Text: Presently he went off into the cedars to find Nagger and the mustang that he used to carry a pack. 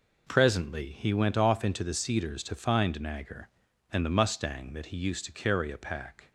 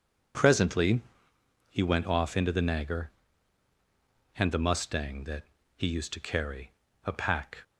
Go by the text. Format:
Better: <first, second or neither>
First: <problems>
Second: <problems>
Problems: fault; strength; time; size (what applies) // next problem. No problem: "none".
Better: first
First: none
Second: pauses between "Presently" and "he"; noticeable; at 0.9 s; 0.70 s long // skips "cedars to find"; at 2.5 s // pauses between "that" and "he"; slight; at 5.4 s; 0.30 s long // pauses between "carry" and "a"; slight; at 6.7 s; 0.34 s long